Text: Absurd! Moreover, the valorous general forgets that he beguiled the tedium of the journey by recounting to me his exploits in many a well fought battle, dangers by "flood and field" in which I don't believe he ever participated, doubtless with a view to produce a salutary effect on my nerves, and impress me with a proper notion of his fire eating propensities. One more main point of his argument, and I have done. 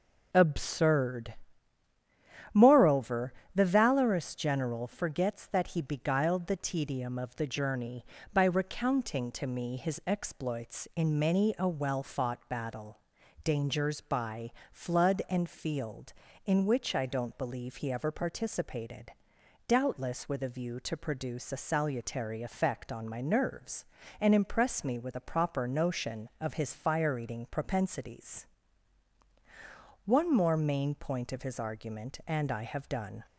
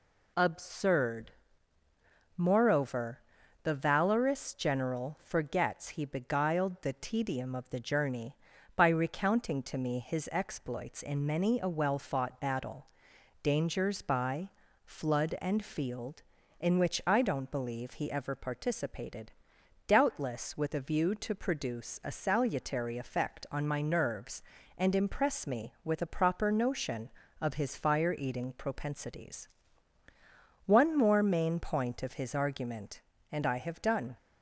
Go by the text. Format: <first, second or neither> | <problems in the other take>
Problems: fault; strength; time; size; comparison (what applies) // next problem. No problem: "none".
first | skips "that"; at 5.9 s // pauses between "by" and "flood"; slight; at 14.5 s; 0.34 s long; slight in the first